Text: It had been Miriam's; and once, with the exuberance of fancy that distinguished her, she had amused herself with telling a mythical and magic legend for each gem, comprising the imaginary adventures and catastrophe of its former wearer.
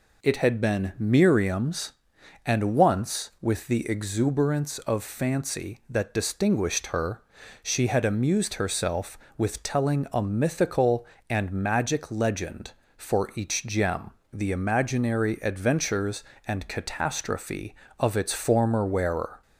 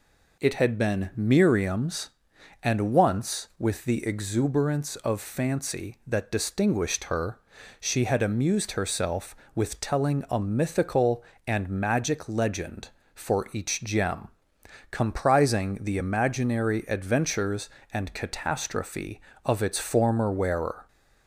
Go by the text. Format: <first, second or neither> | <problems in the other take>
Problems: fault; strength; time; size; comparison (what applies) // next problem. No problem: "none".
second | skips "comprising"; at 14.2 s